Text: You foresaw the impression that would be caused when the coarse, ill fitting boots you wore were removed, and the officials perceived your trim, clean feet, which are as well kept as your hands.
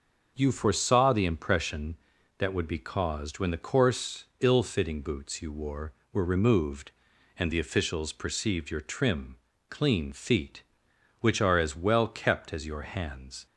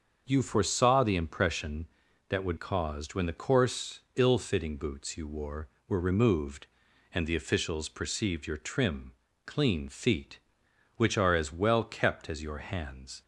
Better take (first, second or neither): first